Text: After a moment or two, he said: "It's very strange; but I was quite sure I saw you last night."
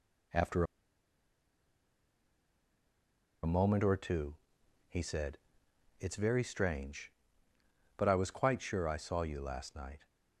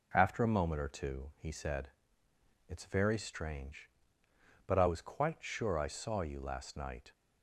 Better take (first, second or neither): second